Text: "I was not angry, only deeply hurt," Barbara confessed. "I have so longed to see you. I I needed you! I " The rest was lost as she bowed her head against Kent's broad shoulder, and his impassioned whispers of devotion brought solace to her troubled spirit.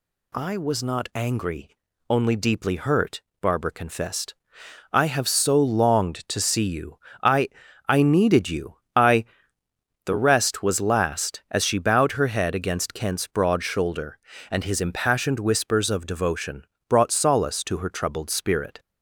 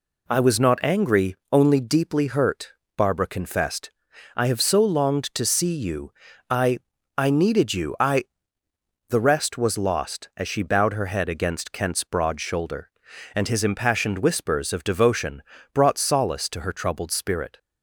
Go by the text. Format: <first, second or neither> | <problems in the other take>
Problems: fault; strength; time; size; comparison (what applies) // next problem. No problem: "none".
second | pauses between "I" and "I"; at 7.4 s; 0.38 s long; also in the second // says "last" for "lost"; at 10.8 s // pauses between "devotion" and "brought"; slight; at 16.6 s; 0.24 s long; slight in the second